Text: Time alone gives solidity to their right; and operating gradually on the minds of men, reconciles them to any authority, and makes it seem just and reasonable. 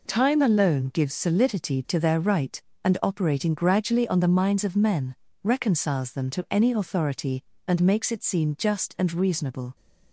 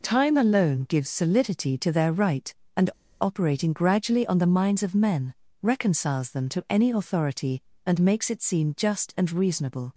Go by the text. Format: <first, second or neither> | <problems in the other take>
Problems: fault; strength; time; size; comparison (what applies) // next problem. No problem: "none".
first | pauses between "and" and "operating"; slight; at 2.8 s; 0.32 s long